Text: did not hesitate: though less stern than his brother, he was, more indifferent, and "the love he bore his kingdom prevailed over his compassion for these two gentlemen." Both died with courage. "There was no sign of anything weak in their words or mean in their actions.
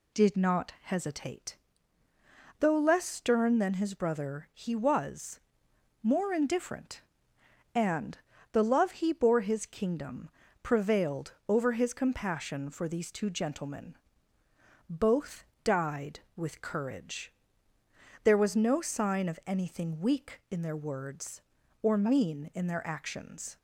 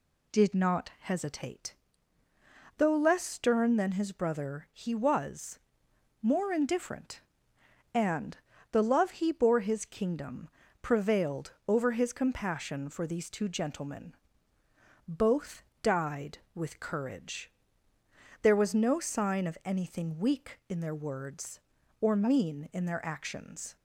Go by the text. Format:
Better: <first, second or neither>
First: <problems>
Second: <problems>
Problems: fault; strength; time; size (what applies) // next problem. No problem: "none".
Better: neither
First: pauses between "and" and "the"; slight; at 8.1 s; 0.34 s long // pauses between "kingdom" and "prevailed"; slight; at 10.2 s; 0.34 s long // pauses between "Both" and "died"; slight; at 15.4 s; 0.18 s long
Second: pauses between "and" and "the"; slight; at 8.3 s; 0.34 s long // pauses between "kingdom" and "prevailed"; slight; at 10.4 s; 0.34 s long // pauses between "Both" and "died"; slight; at 15.6 s; 0.18 s long